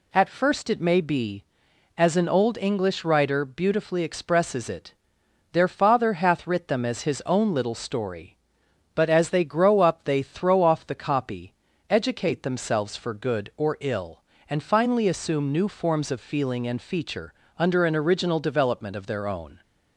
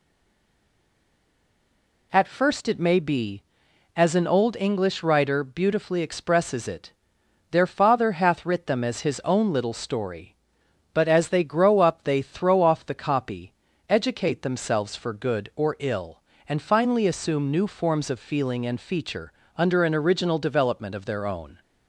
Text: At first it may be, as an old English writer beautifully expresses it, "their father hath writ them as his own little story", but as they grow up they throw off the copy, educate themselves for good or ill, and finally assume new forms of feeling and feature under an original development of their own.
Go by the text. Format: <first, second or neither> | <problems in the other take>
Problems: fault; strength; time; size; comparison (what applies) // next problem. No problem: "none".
first | stays silent before the first word; until 2.1 s; 2.1 s long // pauses between "feature" and "under"; slight; at 19.3 s; 0.24 s long; slight in the first